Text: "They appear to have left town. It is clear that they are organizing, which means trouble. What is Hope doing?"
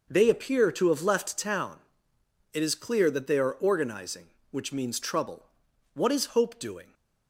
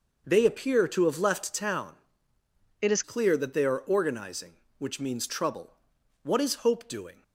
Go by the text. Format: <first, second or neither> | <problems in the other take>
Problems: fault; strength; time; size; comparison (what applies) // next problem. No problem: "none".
first | changes voice from "It" to "is"; from 2.8 to 3.0 s; 0.2 s long